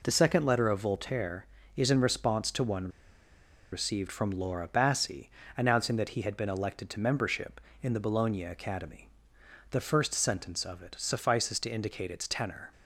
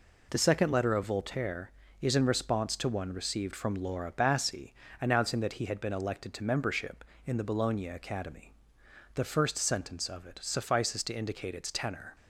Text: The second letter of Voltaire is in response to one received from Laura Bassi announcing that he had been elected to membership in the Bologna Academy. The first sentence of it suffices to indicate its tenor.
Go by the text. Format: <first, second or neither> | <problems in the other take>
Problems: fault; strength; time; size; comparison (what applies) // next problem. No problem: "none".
second | pauses between "one" and "received"; noticeable; at 2.8 s; 0.84 s long // pauses between "Bassi" and "announcing"; slight; at 5.2 s; 0.26 s long; slight in the second